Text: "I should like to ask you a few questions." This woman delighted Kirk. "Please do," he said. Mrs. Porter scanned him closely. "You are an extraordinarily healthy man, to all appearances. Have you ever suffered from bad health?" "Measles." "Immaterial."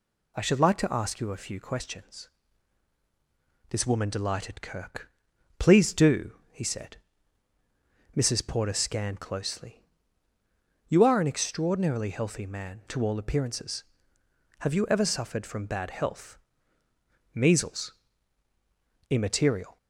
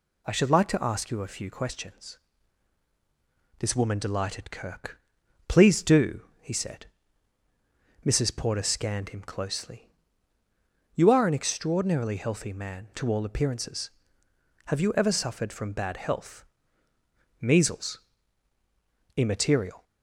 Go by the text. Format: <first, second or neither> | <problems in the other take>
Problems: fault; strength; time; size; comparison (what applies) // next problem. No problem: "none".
second | skips "him"; at 9.1 s